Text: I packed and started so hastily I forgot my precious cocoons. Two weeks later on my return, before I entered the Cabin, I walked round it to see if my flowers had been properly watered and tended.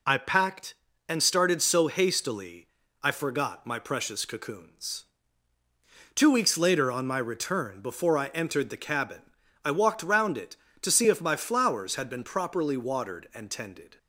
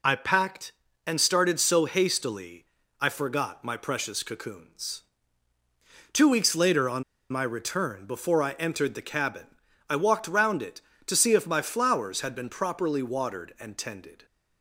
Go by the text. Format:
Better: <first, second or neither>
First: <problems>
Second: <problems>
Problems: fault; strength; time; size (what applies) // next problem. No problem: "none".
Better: first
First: pauses between "hastily" and "I"; slight; at 2.6 s; 0.34 s long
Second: pauses between "hastily" and "I"; slight; at 2.6 s; 0.34 s long // pauses between "on" and "my"; slight; at 7.0 s; 0.27 s long